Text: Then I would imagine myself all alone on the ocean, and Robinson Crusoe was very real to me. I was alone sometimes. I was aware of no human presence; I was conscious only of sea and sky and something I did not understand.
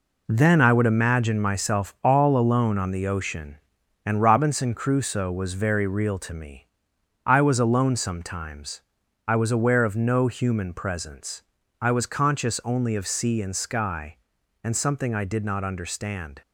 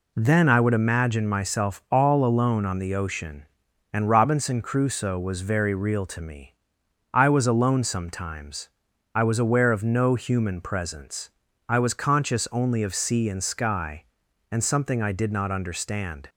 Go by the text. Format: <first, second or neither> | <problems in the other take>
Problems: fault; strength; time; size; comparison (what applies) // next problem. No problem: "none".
second | gets quieter; strong; throughout; 8 dB